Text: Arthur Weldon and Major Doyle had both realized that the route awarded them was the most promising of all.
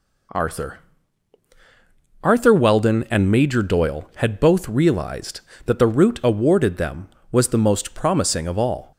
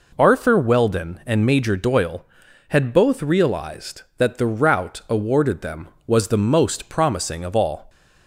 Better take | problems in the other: second | says "Arthur" twice; at 2.2 s

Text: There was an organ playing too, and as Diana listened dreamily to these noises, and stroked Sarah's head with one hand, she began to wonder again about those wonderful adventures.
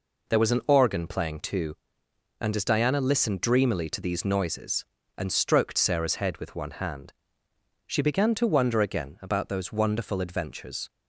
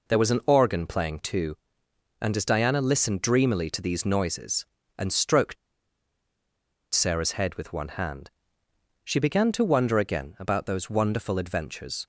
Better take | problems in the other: first | pauses between "stroked" and "Sarah's"; strong; at 5.5 s; 1.3 s long

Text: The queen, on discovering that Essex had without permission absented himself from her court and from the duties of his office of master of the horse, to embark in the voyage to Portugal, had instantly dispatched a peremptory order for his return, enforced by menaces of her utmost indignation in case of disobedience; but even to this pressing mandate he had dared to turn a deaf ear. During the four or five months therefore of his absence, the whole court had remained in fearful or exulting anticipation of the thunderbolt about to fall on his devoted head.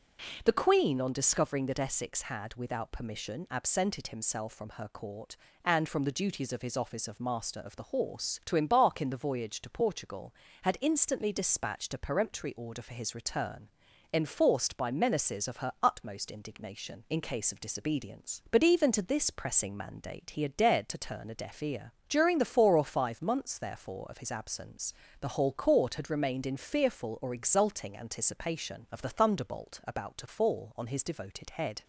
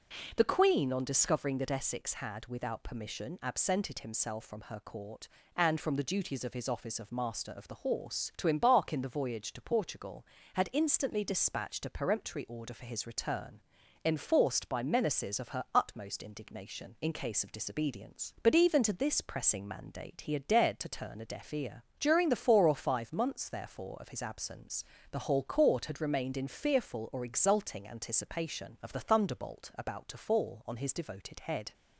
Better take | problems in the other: neither | none

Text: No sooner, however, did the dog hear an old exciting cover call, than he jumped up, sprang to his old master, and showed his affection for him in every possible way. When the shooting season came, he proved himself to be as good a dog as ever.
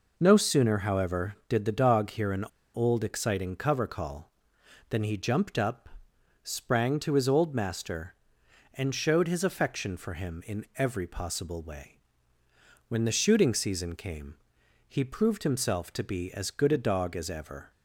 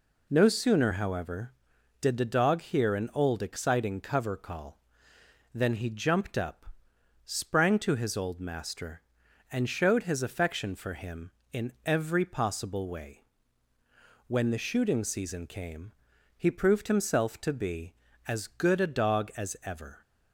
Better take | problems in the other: second | pauses between "an" and "old"; slight; at 2.4 s; 0.28 s long

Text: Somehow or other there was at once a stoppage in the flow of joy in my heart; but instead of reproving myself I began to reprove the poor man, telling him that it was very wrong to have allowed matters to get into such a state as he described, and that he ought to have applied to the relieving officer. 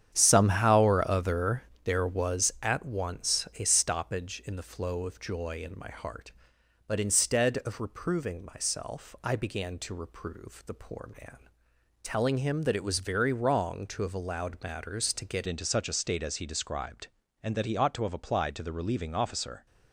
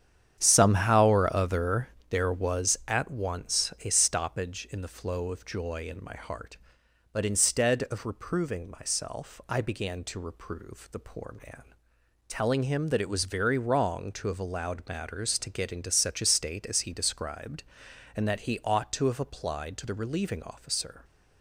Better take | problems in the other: second | starts louder than the rest; strong; until 1.1 s; 9 dB; strong in the second // pauses between "other" and "there"; slight; at 1.6 s; 0.22 s long; slight in the second // changes voice at "into"; from 15.4 s on; 4.2 s long

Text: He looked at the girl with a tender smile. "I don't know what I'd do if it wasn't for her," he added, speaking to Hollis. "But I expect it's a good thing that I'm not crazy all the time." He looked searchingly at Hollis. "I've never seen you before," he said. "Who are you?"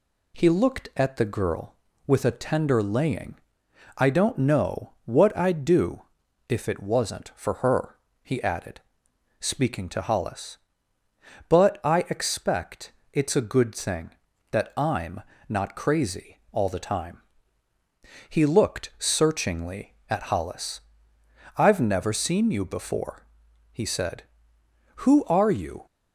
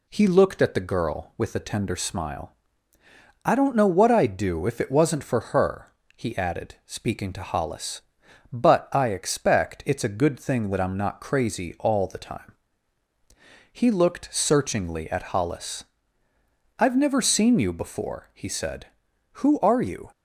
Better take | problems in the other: second | says "laying" for "smile"; at 2.8 s // pauses between "do" and "if"; noticeable; at 6.0 s; 0.48 s long // pauses between "expect" and "it's"; slight; at 12.9 s; 0.22 s long // pauses between "I'm" and "not"; slight; at 15.2 s; 0.26 s long

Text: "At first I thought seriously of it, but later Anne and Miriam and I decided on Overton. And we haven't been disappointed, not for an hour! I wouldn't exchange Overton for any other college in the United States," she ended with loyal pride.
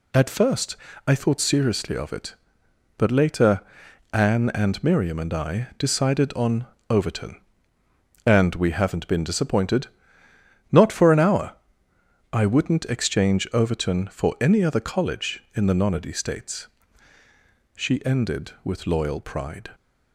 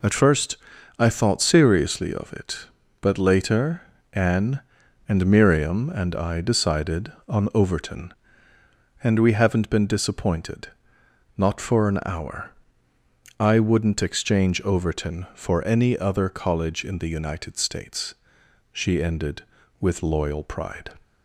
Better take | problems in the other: second | pauses between "first" and "I"; slight; at 0.7 s; 0.30 s long; also in the second // pauses between "later" and "Anne"; noticeable; at 3.6 s; 0.50 s long; slight in the second // pauses between "on" and "Overton"; slight; at 6.6 s; 0.24 s long // says "Nonody" for "United"; at 15.7 s

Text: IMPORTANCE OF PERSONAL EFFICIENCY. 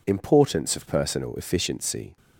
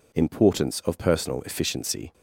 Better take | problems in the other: neither | none

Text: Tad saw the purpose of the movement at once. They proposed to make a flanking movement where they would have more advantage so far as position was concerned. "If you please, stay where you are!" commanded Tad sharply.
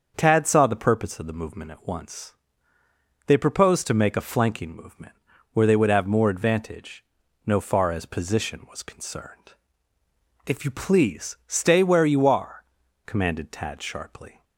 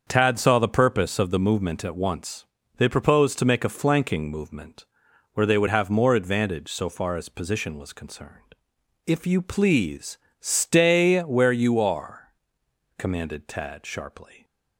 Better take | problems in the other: second | starts louder than the rest; until 1.1 s; 7 dB; also in the second // pauses between "movement" and "where"; at 5.1 s; 0.40 s long; noticeable in the second // says "no" for "so"; at 7.4 s

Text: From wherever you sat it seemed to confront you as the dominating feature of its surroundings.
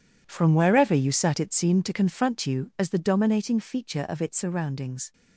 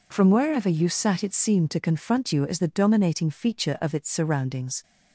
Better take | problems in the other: second | gets quieter; strong; throughout; 13.5 dB

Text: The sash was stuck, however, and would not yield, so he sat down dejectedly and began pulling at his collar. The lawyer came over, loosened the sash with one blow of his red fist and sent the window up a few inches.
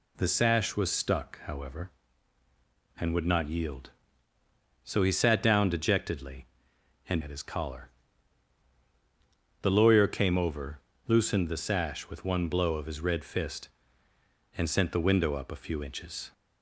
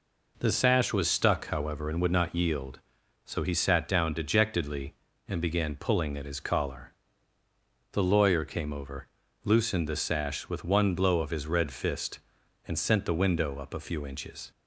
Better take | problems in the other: second | skips "began pulling"; at 7.2 s

